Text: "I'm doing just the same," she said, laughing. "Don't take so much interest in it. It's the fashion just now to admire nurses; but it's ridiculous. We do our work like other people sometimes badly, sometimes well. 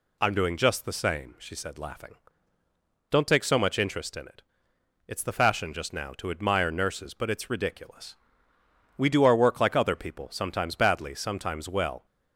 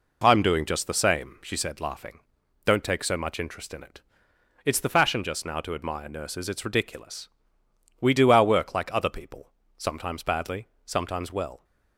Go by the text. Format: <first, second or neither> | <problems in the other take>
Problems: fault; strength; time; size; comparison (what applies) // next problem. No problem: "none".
first | skips "but"; at 6.4 s // pauses between "people" and "sometimes"; slight; at 9.4 s; 0.28 s long